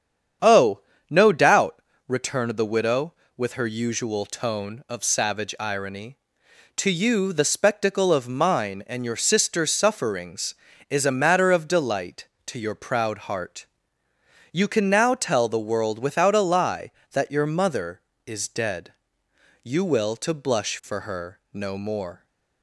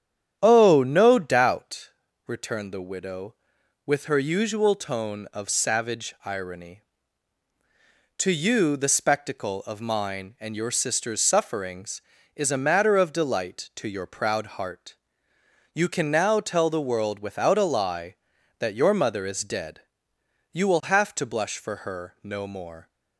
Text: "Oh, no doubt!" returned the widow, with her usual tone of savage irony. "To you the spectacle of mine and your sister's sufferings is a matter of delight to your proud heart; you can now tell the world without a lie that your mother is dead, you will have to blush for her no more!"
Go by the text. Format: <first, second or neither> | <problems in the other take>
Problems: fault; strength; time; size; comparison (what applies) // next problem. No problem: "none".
second | starts louder than the rest; strong; until 1.7 s; 8 dB; strong in the second // skips "have"; at 20.1 s